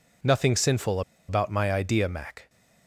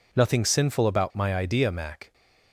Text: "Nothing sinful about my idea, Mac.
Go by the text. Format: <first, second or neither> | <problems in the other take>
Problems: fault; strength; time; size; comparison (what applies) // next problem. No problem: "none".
second | pauses between "sinful" and "about"; slight; at 1.0 s; 0.27 s long